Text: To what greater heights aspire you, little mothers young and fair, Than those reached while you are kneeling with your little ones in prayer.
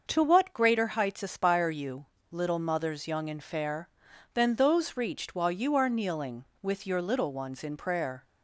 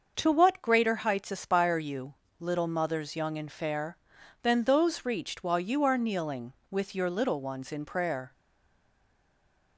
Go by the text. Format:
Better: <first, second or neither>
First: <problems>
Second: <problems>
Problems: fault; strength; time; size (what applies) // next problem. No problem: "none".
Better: first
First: starts louder than the rest; until 1.0 s; 6 dB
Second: starts louder than the rest; until 1.1 s; 6 dB // stays silent after the last word; noticeable; from 8.3 s on; 1.4 s long